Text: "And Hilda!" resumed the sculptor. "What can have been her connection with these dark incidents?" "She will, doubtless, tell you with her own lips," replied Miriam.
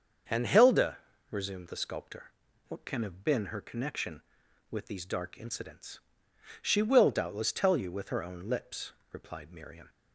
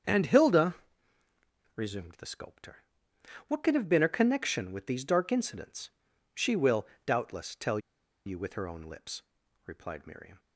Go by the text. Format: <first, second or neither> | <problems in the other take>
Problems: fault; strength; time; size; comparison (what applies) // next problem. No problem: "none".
first | starts louder than the rest; strong; until 2.0 s; 7.5 dB; also in the first // pauses between "tell" and "you"; noticeable; at 7.7 s; 0.47 s long